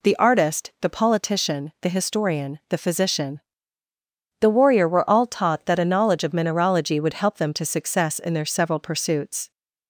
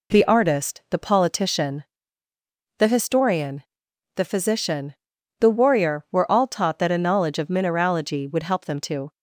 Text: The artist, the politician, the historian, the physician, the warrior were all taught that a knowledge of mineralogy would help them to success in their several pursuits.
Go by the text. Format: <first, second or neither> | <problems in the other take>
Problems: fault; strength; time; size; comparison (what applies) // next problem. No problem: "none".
first | stops before "success in their several pursuits"; at 9.1 s